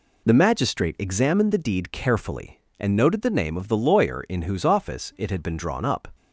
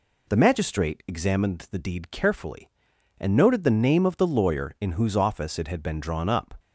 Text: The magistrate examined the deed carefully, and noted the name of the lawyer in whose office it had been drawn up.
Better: neither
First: none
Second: none

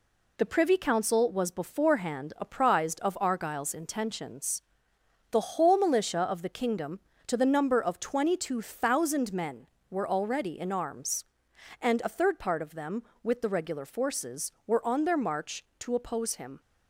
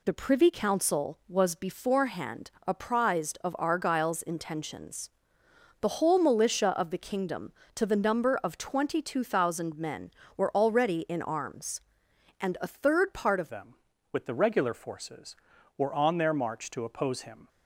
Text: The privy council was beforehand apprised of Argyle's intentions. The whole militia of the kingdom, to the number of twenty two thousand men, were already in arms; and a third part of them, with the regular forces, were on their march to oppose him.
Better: first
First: none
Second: pauses between "beforehand" and "apprised"; slight; at 2.5 s; 0.16 s long // changes voice at "them"; from 13.4 s on; 4.0 s long

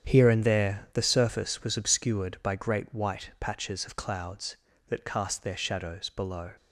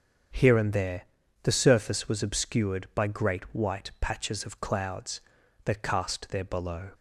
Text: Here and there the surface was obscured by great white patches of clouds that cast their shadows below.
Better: first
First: starts louder than the rest; strong; until 1.1 s; 8.5 dB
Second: starts louder than the rest; strong; until 1.7 s; 7.5 dB // pauses between "there" and "the"; at 1.0 s; 0.40 s long // skips "shadows"; at 6.4 s

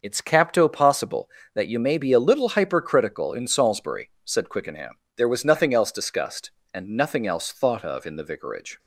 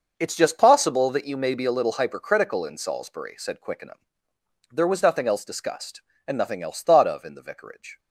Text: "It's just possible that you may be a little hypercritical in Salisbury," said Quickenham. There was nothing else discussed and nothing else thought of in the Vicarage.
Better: second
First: starts louder than the rest; noticeable; until 1.0 s; 6 dB // says "capto" for "just"; at 0.2 s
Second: starts louder than the rest; until 1.1 s; 6 dB

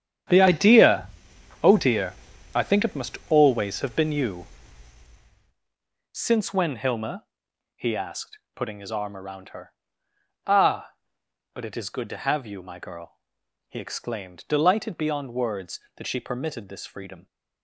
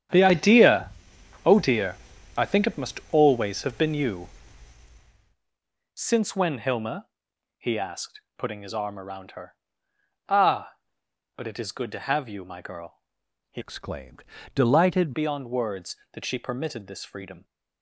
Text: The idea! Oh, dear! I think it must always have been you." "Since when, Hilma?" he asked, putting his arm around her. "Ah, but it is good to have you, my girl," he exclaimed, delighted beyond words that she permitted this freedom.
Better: first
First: starts louder than the rest; strong; until 1.8 s; 9 dB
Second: starts louder than the rest; strong; until 1.6 s; 9 dB // changes voice from "exclaimed" to "delighted"; from 13.5 to 15.1 s; 1.6 s long

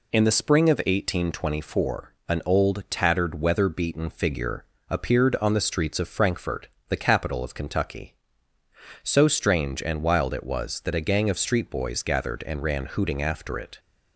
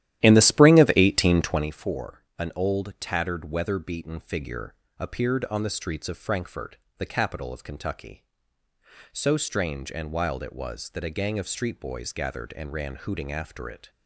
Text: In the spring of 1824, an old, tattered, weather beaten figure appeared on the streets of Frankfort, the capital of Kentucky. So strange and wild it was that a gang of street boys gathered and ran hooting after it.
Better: first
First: pauses between "figure" and "appeared"; slight; at 4.6 s; 0.26 s long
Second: starts louder than the rest; strong; until 1.8 s; 13 dB // pauses between "figure" and "appeared"; slight; at 4.7 s; 0.25 s long

